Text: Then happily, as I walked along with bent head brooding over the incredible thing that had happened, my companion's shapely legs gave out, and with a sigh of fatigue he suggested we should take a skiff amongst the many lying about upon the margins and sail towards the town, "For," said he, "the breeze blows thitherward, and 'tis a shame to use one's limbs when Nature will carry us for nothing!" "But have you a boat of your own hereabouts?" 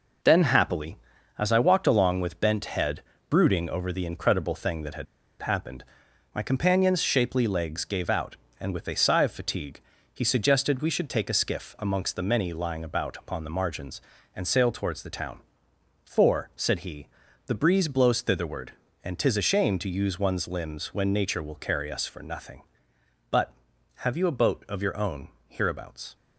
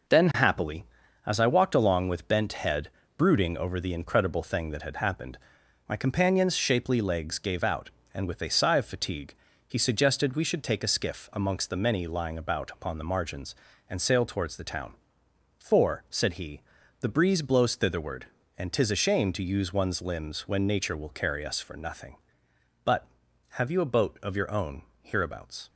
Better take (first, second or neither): second